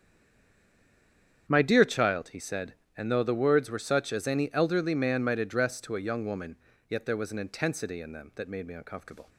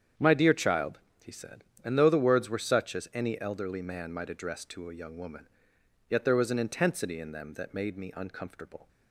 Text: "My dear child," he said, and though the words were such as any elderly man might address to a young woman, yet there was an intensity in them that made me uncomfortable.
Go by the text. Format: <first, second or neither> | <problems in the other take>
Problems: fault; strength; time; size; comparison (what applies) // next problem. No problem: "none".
second | stays silent before the first word; noticeable; until 1.4 s; 1.4 s long // starts louder than the rest; strong; until 2.4 s; 8 dB; strong in the second